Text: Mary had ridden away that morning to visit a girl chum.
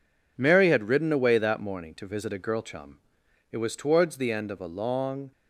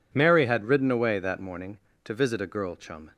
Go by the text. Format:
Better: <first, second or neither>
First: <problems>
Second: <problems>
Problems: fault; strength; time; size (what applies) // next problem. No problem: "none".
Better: second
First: goes on to say "It was towards the end of a long"; strong; from 3.5 s on; 1.8 s long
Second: none